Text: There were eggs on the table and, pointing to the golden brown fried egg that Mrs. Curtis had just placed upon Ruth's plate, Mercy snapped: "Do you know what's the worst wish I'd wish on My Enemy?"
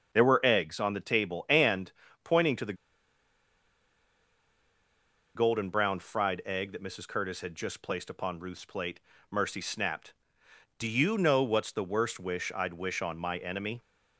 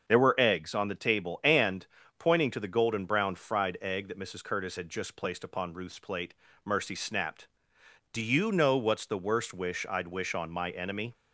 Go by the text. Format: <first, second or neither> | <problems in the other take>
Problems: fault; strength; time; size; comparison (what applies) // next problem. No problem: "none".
second | starts louder than the rest; until 1.1 s; 6 dB; also in the second // pauses between "the" and "golden"; strong; at 2.7 s; 2.6 s long